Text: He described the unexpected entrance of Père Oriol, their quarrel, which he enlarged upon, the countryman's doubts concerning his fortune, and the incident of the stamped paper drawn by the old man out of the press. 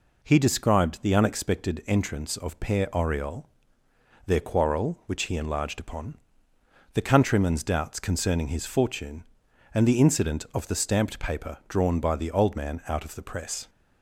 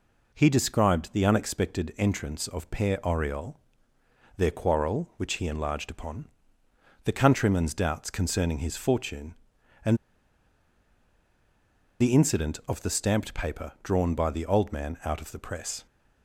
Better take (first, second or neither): first